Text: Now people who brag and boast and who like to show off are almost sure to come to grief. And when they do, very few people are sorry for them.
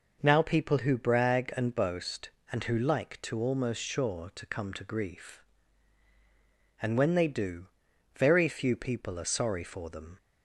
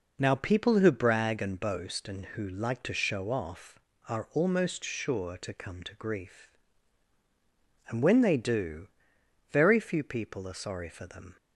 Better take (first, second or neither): second